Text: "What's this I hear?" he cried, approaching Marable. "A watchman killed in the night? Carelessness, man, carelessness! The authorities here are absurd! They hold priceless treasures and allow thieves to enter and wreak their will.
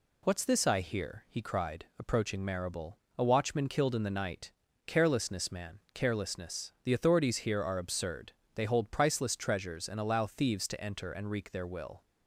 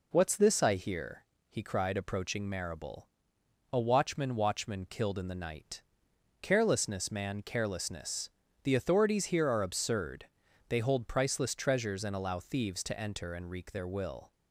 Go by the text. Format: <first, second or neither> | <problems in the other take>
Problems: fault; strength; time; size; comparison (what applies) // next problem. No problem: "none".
first | says "watchman" twice; at 4.3 s